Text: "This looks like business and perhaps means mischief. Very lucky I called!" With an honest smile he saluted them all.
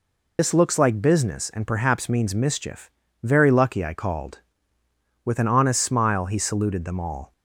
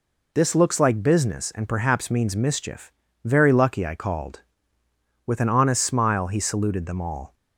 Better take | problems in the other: second | loses the start of "This"; at 0.3 s; 70 ms

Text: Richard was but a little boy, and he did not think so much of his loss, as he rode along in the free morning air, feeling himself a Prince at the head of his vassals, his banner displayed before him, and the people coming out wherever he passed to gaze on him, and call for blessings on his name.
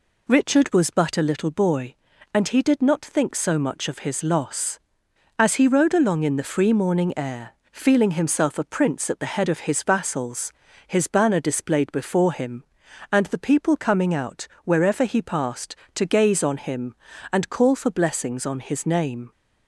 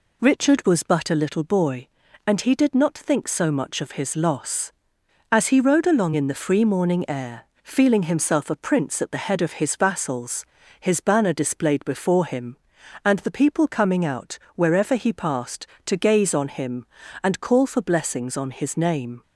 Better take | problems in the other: neither | pauses between "out" and "wherever"; slight; the same in both

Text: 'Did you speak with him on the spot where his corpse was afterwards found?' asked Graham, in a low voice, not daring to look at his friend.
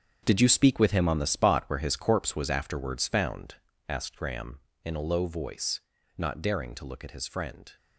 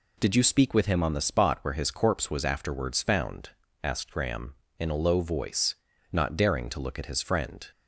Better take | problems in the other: second | gets quieter; strong; throughout; 11.5 dB

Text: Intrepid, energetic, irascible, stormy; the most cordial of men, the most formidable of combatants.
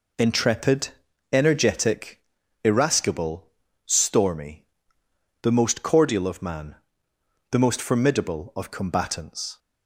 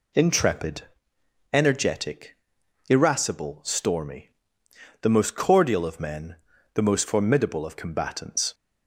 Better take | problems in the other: second | says "man" for "men"; at 6.4 s

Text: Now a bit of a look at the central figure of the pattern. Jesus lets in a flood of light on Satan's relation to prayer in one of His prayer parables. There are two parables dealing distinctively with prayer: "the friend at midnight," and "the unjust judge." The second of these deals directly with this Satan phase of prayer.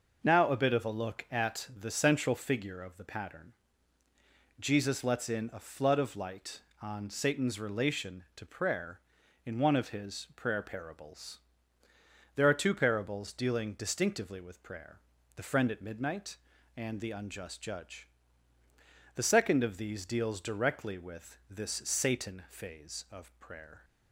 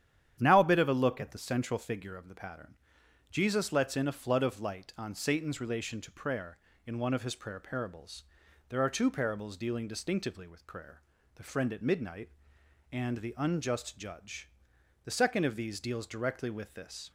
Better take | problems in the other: first | starts louder than the rest; strong; until 1.4 s; 10 dB // stops before "Satan phase of prayer"; at 17.0 s

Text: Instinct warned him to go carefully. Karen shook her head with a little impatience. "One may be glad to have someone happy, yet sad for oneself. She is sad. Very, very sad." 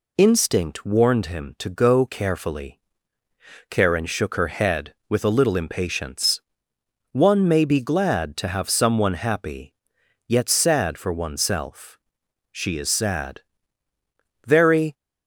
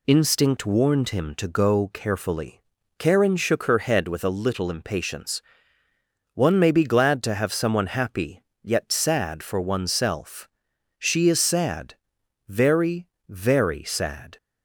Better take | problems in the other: second | stops before "very sad"; at 14.9 s

